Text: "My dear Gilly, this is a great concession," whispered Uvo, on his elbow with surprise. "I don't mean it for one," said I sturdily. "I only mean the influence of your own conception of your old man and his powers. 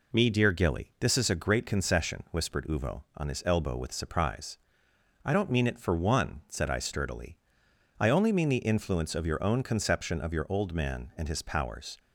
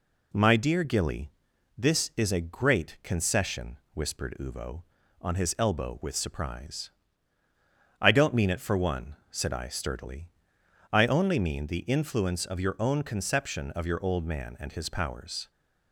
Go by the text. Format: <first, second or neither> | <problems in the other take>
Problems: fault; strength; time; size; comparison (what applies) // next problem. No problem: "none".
second | says "Me" for "My"; at 0.1 s